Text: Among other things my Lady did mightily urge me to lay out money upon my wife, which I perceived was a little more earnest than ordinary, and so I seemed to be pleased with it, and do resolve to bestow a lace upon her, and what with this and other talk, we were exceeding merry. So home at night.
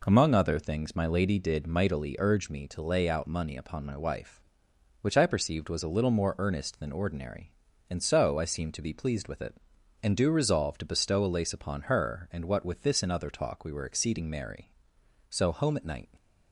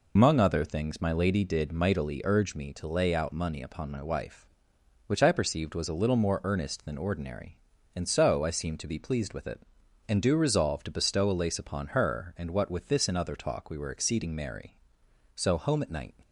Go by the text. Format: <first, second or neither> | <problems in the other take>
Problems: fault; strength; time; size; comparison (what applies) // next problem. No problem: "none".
first | loses the start of "Among"; at 0.1 s; 80 ms